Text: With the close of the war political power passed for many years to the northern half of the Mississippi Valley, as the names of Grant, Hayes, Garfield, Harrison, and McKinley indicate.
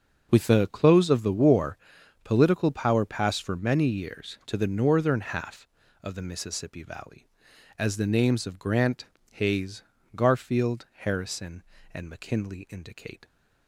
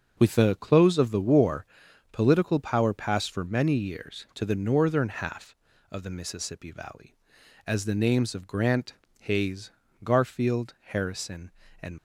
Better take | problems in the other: first | starts louder than the rest; until 1.1 s; 6.5 dB; noticeable in the first // pauses between "war" and "political"; noticeable; at 1.6 s; 0.46 s long; noticeable in the first // stops before "McKinley indicate"; at 11.9 s

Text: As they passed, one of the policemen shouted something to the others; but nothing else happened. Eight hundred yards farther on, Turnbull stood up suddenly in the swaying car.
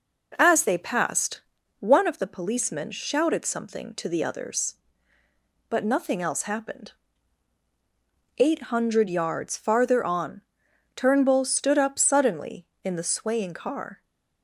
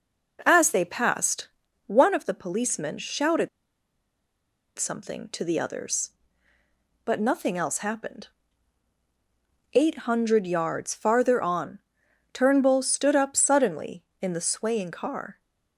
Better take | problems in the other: first | pauses between "shouted" and "something"; strong; at 3.4 s; 1.3 s long

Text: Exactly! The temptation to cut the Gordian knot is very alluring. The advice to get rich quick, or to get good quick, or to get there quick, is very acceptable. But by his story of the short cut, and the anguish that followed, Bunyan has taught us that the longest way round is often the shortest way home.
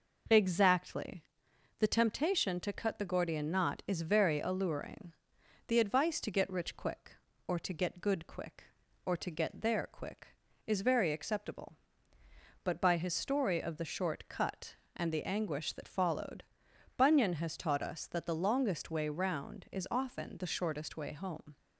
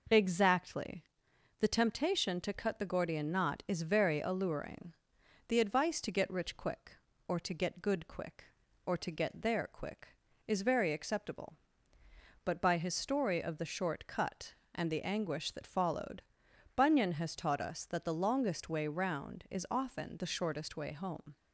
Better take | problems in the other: neither | none

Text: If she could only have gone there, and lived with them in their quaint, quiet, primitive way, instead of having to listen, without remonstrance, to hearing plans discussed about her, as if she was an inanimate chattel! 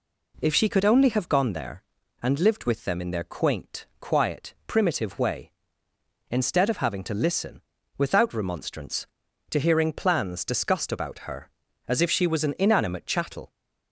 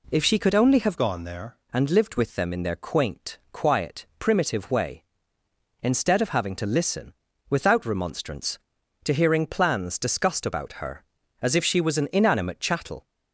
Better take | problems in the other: first | changes voice from "gone" to "there"; from 0.9 to 1.5 s; 0.6 s long

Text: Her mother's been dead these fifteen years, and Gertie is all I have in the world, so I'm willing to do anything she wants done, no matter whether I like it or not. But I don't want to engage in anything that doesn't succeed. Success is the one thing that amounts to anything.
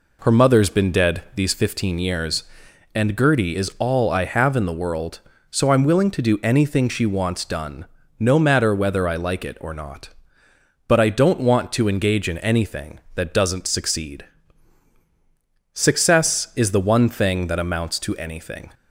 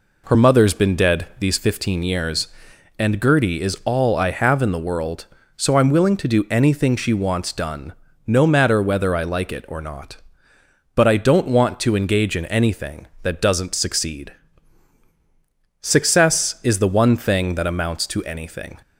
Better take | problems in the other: neither | none

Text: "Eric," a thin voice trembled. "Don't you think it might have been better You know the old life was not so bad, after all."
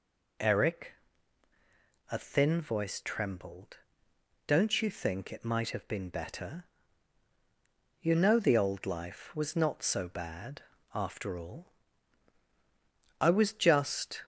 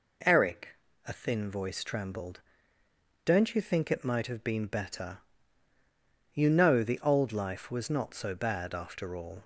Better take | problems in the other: second | pauses between "better" and "You"; strong; at 6.6 s; 1.3 s long; also in the second // goes on to say "I was just"; noticeable; from 13.1 s on; 1.0 s long

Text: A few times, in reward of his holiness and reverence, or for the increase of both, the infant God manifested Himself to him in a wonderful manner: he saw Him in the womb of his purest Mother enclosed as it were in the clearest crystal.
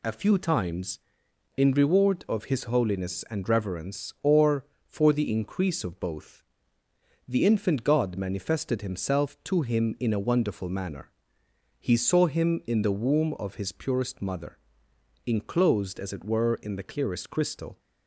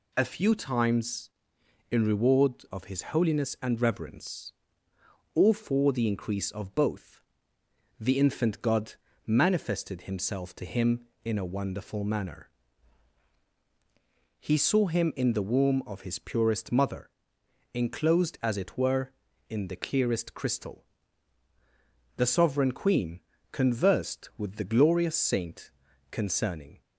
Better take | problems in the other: first | pauses between "his" and "holiness"; slight; at 3.0 s; 0.16 s long // pauses between "God" and "manifested"; slight; at 8.9 s; 0.32 s long // pauses between "Mother" and "enclosed"; noticeable; at 17.0 s; 0.66 s long; noticeable in the first // goes on to say "The sovereign Queen conversed with the glorious saint concerning"; strong; from 22.1 s on; 4.6 s long

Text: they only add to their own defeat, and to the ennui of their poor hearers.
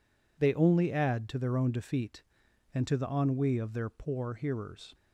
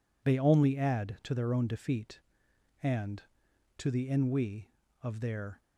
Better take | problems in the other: first | stops before "poor hearers"; at 5.6 s

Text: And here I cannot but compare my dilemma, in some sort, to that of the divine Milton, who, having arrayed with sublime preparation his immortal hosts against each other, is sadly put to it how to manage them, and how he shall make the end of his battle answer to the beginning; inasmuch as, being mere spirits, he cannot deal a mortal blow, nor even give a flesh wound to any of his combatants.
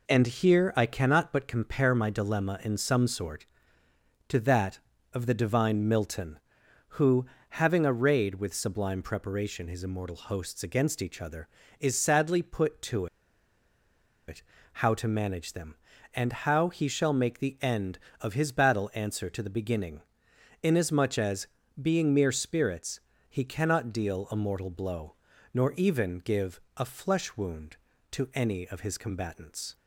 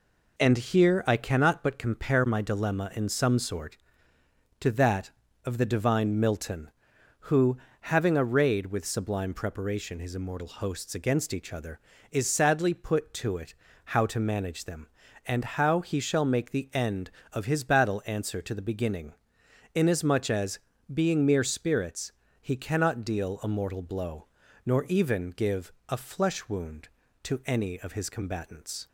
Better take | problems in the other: second | pauses between "to" and "it"; at 13.0 s; 1.2 s long // pauses between "it" and "how"; slight; at 14.4 s; 0.30 s long; slight in the second // pauses between "give" and "a"; slight; at 26.5 s; 0.18 s long; slight in the second

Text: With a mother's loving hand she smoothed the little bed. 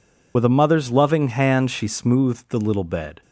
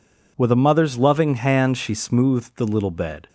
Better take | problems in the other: second | loses the start of "With"; at 0.3 s; 60 ms

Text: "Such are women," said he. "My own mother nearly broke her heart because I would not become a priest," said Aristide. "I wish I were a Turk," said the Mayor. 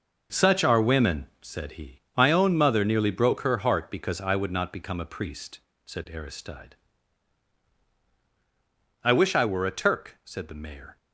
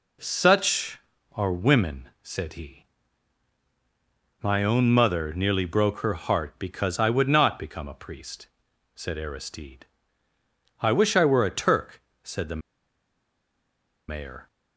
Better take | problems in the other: first | pauses between "the" and "Mayor"; strong; at 12.5 s; 1.4 s long

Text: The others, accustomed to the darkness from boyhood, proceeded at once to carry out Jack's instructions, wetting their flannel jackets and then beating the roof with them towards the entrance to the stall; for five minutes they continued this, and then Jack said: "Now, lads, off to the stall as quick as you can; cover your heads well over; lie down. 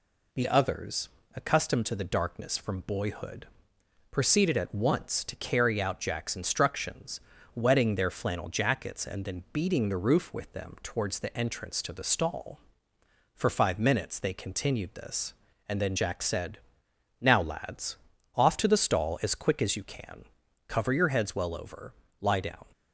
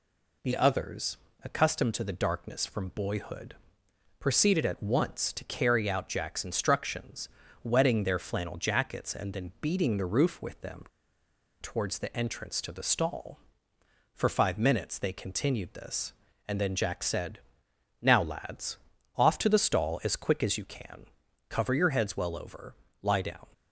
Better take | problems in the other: first | pauses between "them" and "towards"; noticeable; at 10.8 s; 0.76 s long

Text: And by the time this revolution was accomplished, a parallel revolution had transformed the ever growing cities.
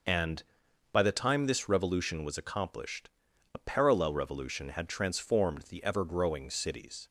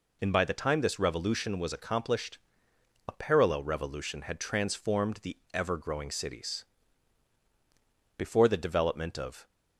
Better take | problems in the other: first | pauses between "the" and "ever"; slight; at 5.3 s; 0.16 s long // goes on to say "Before the development of"; noticeable; from 8.3 s on; 1.1 s long

